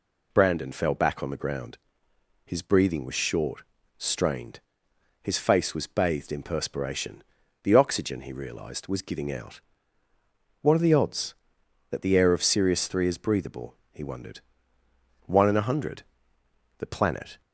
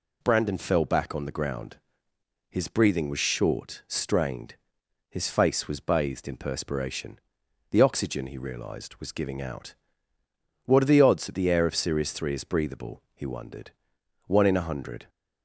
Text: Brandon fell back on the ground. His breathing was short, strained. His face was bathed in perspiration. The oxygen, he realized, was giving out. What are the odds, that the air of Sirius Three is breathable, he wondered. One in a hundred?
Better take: second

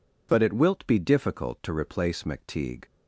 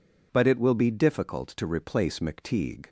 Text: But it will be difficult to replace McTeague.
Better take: second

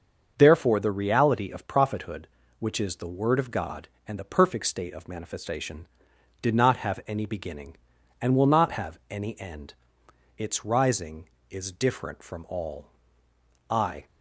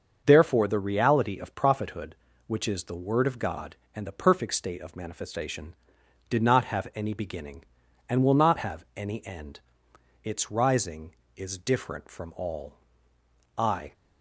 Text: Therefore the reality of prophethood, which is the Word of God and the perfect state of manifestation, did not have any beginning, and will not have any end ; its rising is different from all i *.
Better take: neither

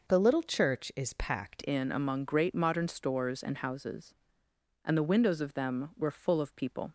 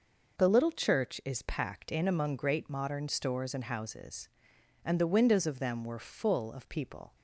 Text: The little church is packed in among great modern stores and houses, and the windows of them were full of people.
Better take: second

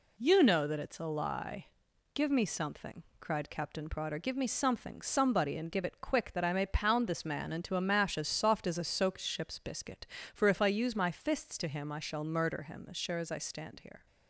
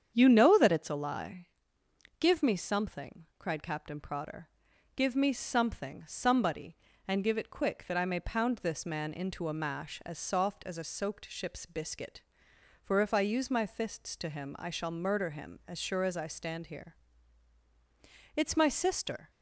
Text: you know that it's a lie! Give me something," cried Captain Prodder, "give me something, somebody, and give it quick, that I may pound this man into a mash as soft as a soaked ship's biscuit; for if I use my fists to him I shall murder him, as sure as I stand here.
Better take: first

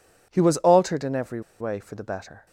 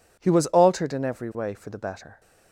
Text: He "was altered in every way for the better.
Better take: second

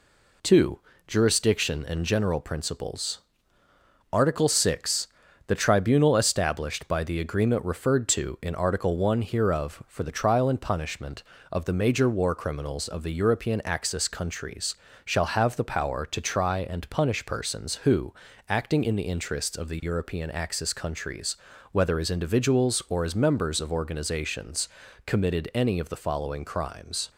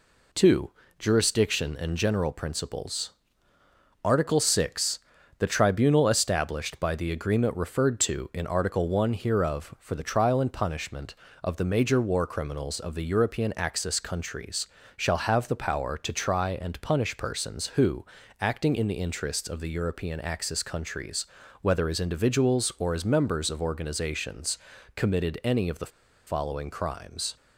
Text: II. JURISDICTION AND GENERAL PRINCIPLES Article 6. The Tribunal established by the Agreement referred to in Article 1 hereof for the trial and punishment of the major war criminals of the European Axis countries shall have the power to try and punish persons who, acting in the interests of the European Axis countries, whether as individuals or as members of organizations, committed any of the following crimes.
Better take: first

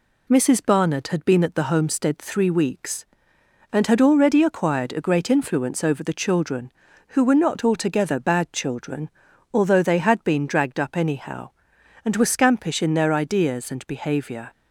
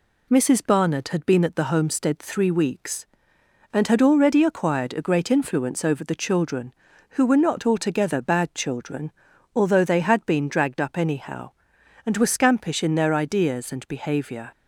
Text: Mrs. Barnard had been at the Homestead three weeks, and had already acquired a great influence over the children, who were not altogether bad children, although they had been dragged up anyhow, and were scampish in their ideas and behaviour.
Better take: neither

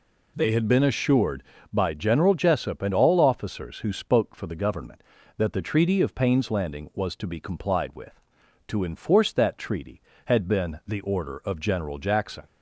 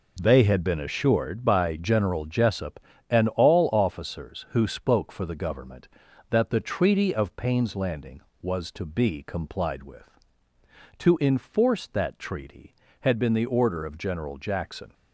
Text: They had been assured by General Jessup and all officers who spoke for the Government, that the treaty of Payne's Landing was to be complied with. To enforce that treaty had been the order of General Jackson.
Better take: neither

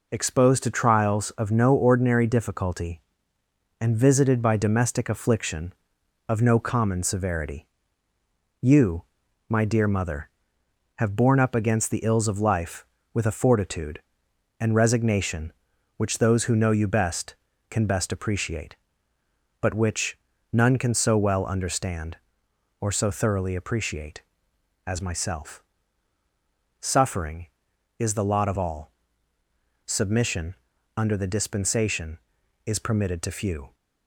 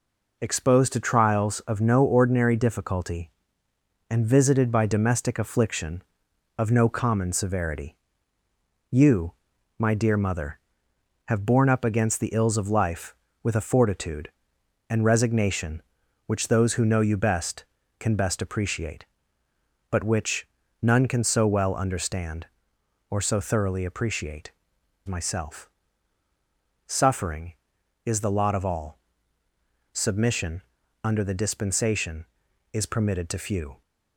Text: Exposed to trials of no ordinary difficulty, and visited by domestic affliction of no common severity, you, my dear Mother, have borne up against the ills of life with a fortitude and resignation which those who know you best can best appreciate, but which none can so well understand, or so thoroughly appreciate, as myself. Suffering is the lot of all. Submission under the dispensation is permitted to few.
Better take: first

